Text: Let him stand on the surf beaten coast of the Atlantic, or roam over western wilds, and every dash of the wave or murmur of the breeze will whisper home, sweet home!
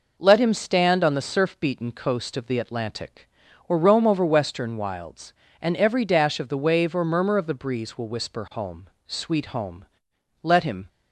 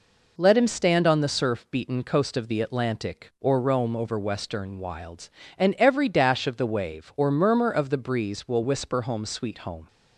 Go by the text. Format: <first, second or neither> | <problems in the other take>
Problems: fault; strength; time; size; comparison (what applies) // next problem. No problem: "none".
second | goes on to say "Let him"; slight; from 10.4 s on; 0.46 s long